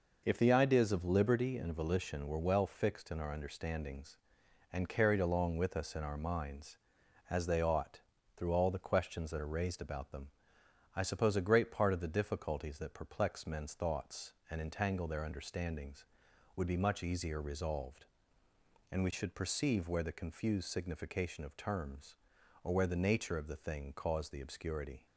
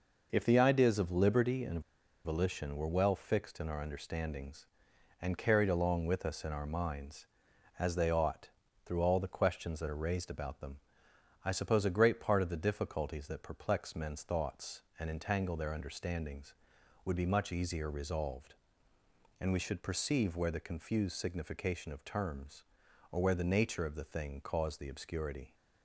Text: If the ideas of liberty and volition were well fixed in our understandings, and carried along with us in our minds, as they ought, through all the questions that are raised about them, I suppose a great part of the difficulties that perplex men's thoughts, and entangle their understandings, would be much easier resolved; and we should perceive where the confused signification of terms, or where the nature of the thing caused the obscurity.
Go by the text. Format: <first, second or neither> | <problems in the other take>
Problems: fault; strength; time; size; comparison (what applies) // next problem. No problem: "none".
first | pauses between "and" and "volition"; at 1.8 s; 0.44 s long